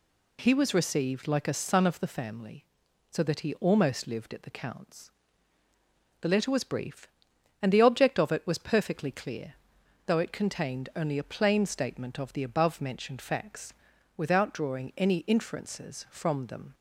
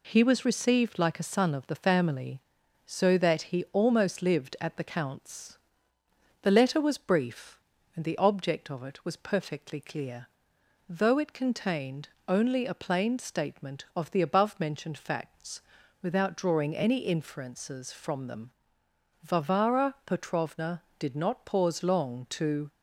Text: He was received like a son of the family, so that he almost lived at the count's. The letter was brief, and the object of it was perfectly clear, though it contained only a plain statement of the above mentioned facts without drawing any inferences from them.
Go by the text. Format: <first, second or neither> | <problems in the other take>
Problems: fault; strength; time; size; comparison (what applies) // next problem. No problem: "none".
first | pauses between "contained" and "only"; slight; at 12.0 s; 0.18 s long // pauses between "facts" and "without"; at 15.5 s; 0.42 s long; also in the first // goes on to say "Varvara Petrovna did not pause long to"; strong; from 19.2 s on; 3.4 s long